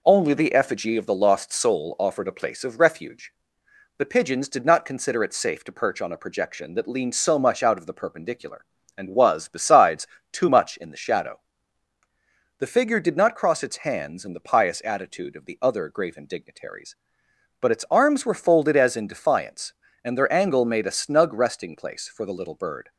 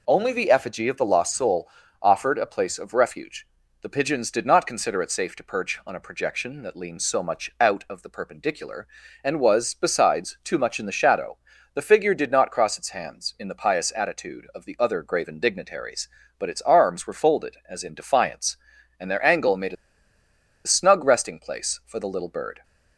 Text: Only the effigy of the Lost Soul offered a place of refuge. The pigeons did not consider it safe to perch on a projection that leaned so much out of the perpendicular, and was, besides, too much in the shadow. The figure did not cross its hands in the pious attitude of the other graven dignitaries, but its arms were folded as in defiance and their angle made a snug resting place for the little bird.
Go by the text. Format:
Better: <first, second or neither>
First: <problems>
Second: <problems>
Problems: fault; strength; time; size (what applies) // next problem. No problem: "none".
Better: first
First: none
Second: pauses between "Soul" and "offered"; slight; at 1.6 s; 0.34 s long // pauses between "a" and "snug"; noticeable; at 19.7 s; 0.91 s long